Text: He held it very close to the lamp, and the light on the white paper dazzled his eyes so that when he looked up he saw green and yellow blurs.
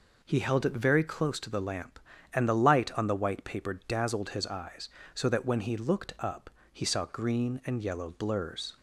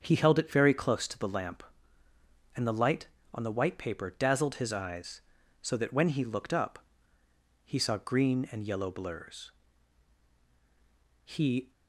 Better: first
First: pauses between "up" and "he"; slight; at 6.4 s; 0.24 s long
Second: starts louder than the rest; until 1.0 s; 7 dB // pauses between "up" and "he"; noticeable; at 6.7 s; 0.84 s long // goes on to say "He"; slight; from 11.2 s on; 0.48 s long

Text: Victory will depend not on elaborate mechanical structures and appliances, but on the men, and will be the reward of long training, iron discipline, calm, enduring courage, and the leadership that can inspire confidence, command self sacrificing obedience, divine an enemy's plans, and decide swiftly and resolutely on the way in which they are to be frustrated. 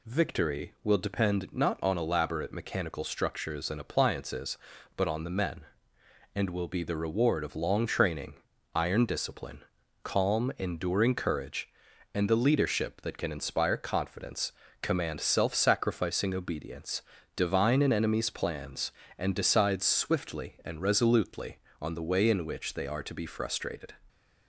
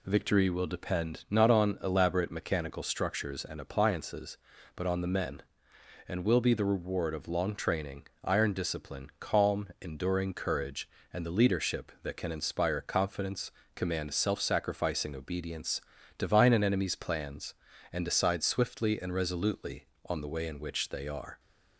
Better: first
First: none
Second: stops before "to be frustrated"; at 21.3 s

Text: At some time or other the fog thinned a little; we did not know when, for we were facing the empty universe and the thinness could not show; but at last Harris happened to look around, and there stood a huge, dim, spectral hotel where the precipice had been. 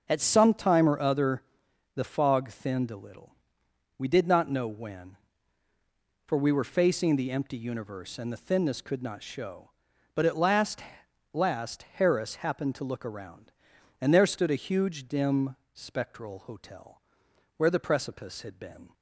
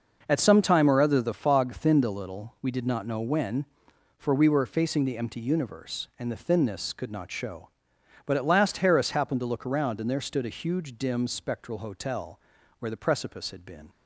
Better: second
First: starts louder than the rest; until 1.1 s; 6 dB // pauses between "other" and "the"; noticeable; at 1.4 s; 0.52 s long // says "last" twice; at 11.3 s // pauses between "hotel" and "where"; noticeable; at 16.9 s; 0.56 s long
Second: pauses between "hotel" and "where"; at 12.3 s; 0.40 s long

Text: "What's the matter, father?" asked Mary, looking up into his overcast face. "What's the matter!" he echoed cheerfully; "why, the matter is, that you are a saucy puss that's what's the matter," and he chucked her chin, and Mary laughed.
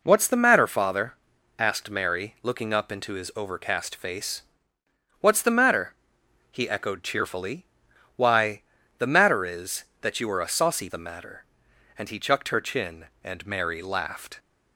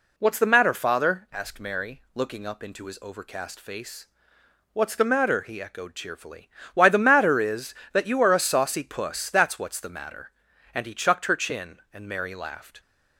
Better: second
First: skips "puss that's what's"; at 10.8 s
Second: none

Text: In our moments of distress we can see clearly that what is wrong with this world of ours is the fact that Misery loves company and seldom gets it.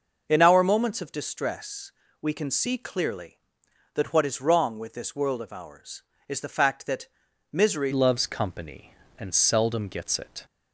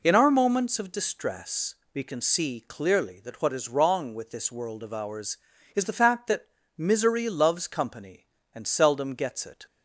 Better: second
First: pauses between "distress" and "we"; slight; at 1.9 s; 0.28 s long // pauses between "that" and "Misery"; noticeable; at 7.0 s; 0.46 s long // changes voice at "loves"; from 7.9 s on; 2.5 s long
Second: pauses between "distress" and "we"; slight; at 1.7 s; 0.18 s long // pauses between "that" and "Misery"; slight; at 6.4 s; 0.32 s long

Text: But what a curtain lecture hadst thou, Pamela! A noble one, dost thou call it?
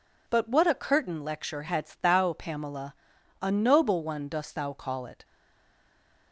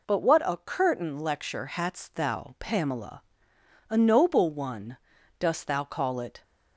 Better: second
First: stays silent after the last word; from 5.2 s on; 1.1 s long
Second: none

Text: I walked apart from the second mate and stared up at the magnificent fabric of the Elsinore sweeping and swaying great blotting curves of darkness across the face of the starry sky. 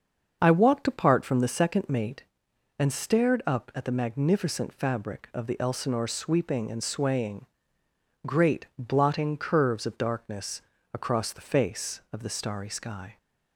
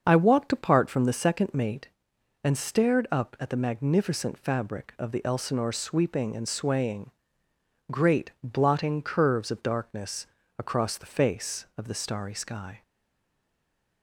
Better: first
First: starts louder than the rest; until 1.4 s; 6.5 dB // pauses between "swaying" and "great"; noticeable; at 7.4 s; 0.80 s long // pauses between "darkness" and "across"; slight; at 10.6 s; 0.32 s long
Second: starts louder than the rest; until 1.0 s; 6.5 dB // pauses between "swaying" and "great"; noticeable; at 7.0 s; 0.80 s long // pauses between "darkness" and "across"; slight; at 10.2 s; 0.32 s long // stays silent after the last word; noticeable; from 12.8 s on; 1.2 s long

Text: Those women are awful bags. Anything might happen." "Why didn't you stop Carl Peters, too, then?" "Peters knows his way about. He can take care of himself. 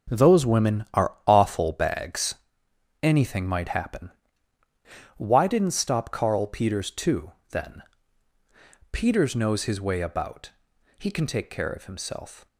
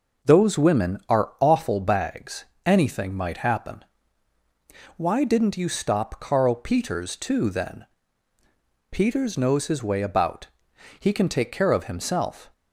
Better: second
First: skips "you"; at 5.8 s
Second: none

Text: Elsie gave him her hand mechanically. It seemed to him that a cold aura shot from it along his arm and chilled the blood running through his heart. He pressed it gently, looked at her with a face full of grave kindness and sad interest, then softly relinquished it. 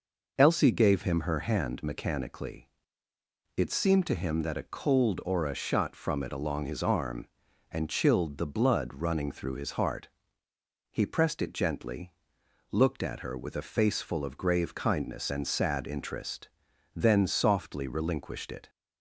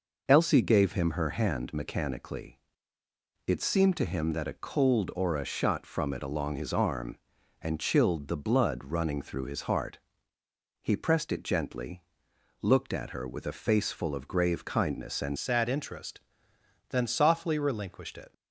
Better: first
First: none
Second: changes voice at "sad"; from 15.3 s on; 3.0 s long

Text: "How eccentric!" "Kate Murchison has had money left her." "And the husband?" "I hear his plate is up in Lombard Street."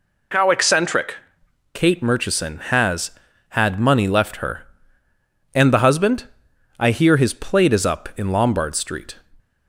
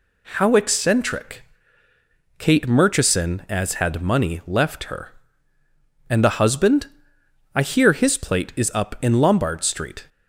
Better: first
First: none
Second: says "as" for "has"; at 3.4 s

